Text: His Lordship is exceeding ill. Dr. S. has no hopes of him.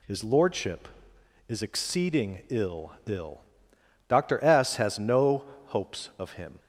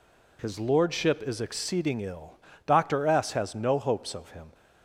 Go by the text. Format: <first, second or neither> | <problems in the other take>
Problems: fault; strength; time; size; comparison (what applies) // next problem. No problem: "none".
second | says "ill" twice; at 3.0 s // pauses between "no" and "hopes"; slight; at 5.4 s; 0.22 s long